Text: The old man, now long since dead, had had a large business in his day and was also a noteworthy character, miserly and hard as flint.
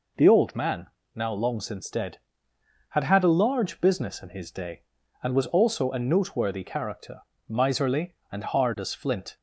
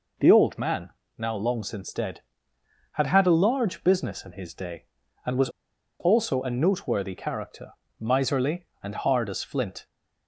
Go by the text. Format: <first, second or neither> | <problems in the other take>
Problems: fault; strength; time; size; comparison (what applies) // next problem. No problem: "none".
first | pauses between "was" and "also"; noticeable; at 5.4 s; 0.50 s long